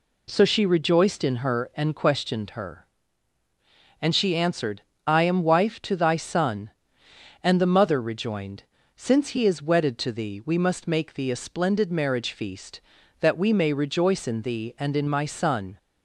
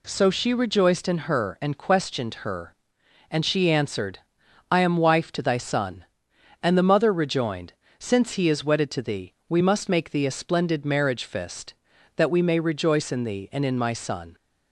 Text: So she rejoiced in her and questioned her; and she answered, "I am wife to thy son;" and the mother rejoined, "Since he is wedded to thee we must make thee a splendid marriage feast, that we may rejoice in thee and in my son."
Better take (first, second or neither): first